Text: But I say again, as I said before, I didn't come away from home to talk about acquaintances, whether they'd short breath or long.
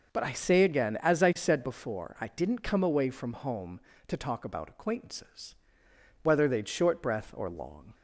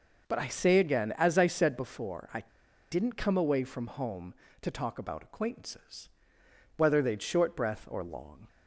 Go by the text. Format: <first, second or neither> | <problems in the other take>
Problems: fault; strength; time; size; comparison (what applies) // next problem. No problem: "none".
first | pauses between "I" and "didn't"; noticeable; at 2.4 s; 0.49 s long